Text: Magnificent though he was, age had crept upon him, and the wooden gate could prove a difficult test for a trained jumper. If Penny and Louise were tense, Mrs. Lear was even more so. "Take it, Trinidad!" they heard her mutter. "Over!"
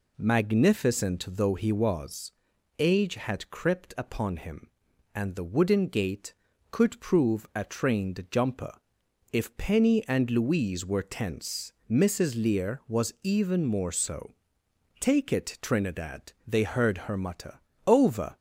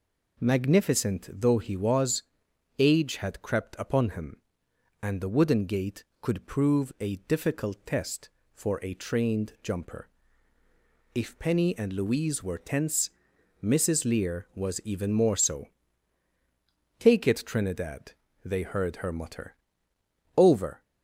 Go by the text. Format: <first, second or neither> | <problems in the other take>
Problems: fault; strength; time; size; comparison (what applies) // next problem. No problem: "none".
second | skips "difficult test for a"; at 7.6 s